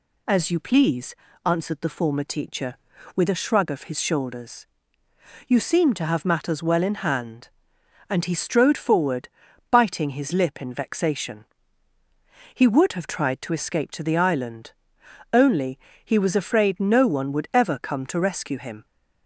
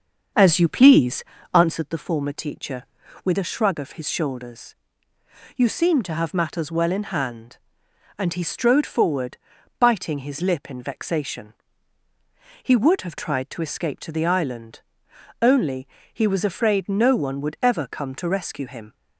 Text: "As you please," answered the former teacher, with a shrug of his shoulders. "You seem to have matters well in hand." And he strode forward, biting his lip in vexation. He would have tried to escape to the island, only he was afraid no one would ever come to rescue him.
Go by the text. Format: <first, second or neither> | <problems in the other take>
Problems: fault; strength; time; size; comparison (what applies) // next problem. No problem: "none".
first | starts louder than the rest; until 1.9 s; 6.5 dB // pauses between "only" and "he"; slight; at 15.8 s; 0.24 s long; slight in the first